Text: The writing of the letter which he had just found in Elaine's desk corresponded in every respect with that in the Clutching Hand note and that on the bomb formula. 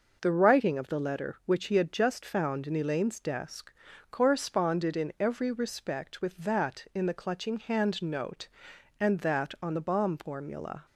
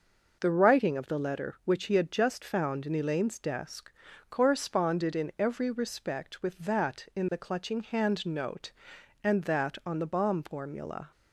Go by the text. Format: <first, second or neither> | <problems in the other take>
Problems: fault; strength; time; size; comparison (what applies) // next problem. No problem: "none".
neither | pauses between "desk" and "corresponded"; the same in both